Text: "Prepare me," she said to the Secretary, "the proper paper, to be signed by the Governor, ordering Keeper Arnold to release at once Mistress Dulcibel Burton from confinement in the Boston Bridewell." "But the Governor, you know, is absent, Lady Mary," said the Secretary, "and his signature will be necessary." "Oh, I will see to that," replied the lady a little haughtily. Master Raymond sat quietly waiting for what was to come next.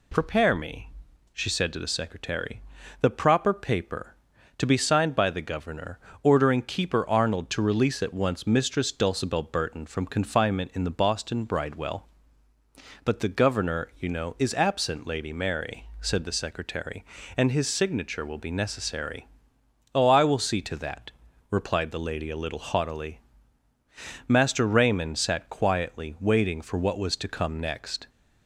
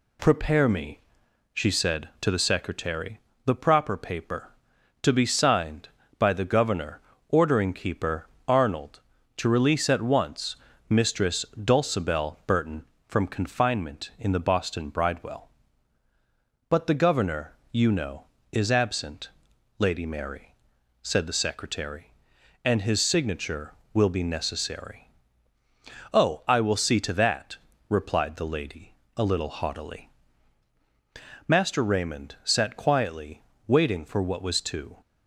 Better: first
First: none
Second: pauses between "Keeper" and "Arnold"; slight; at 8.2 s; 0.20 s long // pauses between "once" and "Mistress"; slight; at 10.5 s; 0.34 s long // pauses between "lady" and "a"; slight; at 28.9 s; 0.24 s long // pauses between "quietly" and "waiting"; slight; at 33.4 s; 0.24 s long // stops before "come next"; at 35.0 s

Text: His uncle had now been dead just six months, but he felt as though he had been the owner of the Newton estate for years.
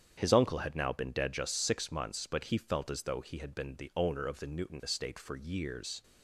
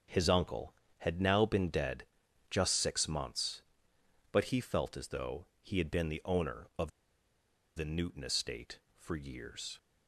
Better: first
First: starts louder than the rest; strong; until 1.1 s; 8.5 dB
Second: starts louder than the rest; strong; until 1.4 s; 7 dB // pauses between "dead" and "just"; noticeable; at 2.0 s; 0.46 s long // pauses between "though" and "he"; slight; at 5.4 s; 0.16 s long // pauses between "of" and "the"; noticeable; at 6.8 s; 0.87 s long

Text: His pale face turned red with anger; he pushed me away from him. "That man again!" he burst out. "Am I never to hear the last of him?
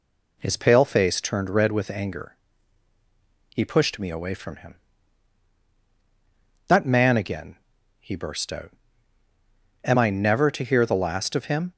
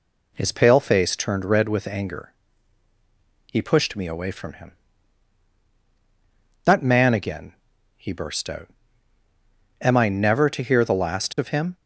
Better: neither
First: none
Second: none

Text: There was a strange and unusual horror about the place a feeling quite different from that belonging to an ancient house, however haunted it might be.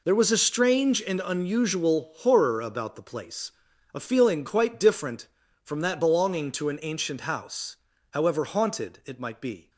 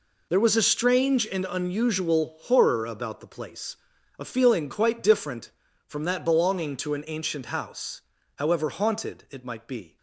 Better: neither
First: pauses between "place" and "a"; at 3.5 s; 0.40 s long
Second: pauses between "place" and "a"; at 3.7 s; 0.40 s long

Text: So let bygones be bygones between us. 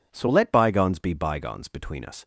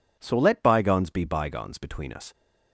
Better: neither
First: none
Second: none

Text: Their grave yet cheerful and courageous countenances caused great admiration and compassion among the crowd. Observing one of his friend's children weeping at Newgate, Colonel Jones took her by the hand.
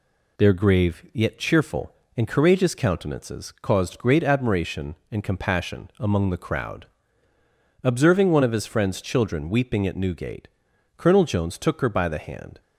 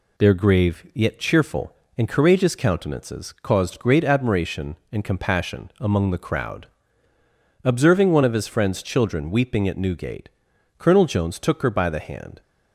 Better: neither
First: none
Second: none

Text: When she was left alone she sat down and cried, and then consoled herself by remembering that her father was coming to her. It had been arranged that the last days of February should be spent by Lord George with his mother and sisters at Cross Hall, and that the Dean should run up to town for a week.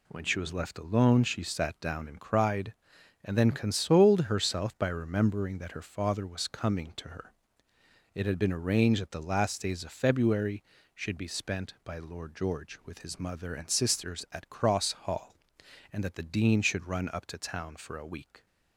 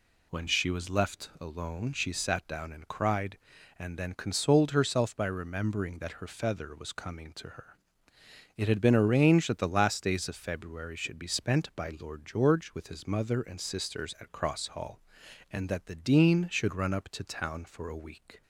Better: first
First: none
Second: says "feather" for "father"; at 6.2 s

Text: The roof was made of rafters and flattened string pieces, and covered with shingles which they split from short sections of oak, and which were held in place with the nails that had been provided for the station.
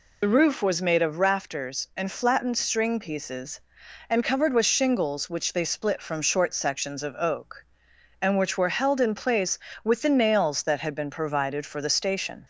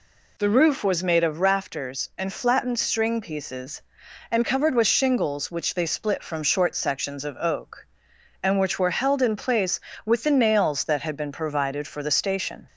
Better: second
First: loses the start of "The"; at 0.2 s; 55 ms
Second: none

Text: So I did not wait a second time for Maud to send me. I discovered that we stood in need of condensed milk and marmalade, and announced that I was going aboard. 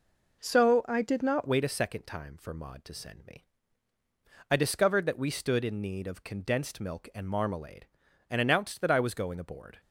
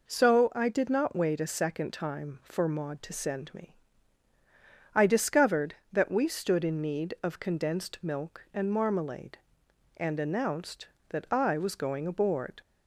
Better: second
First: changes voice at "wait"; from 1.4 s on; 8.3 s long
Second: none

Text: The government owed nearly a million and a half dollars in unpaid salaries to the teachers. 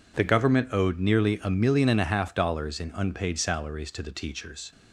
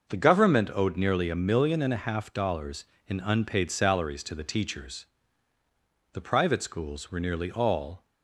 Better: first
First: none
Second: goes on to say "The private schools were nearly all"; strong; from 6.1 s on; 1.9 s long

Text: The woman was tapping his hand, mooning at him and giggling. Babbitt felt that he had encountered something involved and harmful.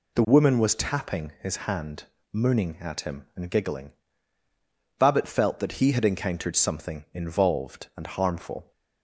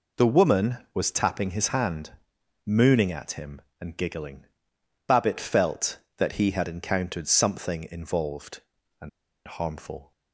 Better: first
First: none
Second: pauses between "and" and "harmful"; at 9.0 s; 0.37 s long

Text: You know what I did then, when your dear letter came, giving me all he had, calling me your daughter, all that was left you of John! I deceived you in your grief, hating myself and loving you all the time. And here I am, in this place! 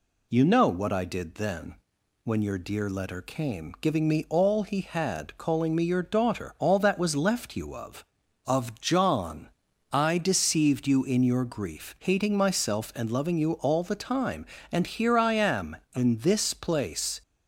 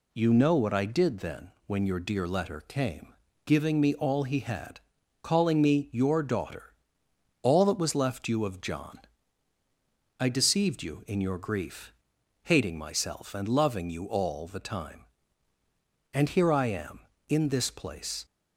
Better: second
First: says "of" twice; at 8.4 s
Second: none

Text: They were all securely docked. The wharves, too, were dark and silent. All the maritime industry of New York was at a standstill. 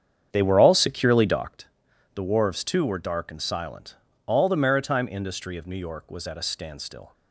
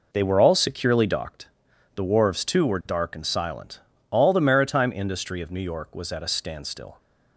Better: second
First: starts louder than the rest; strong; until 1.6 s; 8 dB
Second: none

